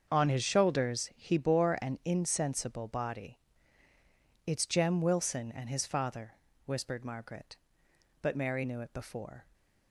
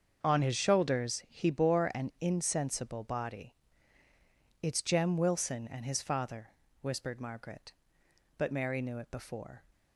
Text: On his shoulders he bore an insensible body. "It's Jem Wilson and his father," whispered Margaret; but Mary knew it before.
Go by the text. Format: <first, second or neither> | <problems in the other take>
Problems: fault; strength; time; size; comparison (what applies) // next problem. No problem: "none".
neither | starts louder than the rest; the same in both